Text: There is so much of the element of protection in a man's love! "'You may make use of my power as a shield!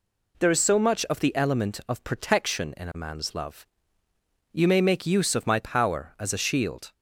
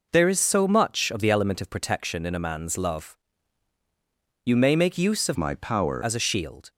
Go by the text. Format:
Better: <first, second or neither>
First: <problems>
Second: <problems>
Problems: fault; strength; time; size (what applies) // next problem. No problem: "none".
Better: first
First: none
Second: changes voice from "my" to "power"; from 5.3 to 6.0 s; 0.7 s long